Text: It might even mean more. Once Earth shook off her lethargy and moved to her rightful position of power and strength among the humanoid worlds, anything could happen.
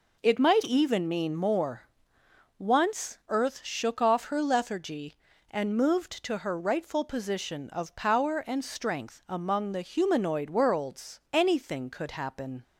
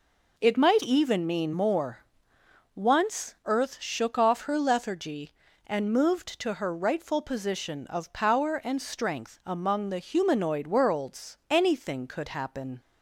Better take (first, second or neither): neither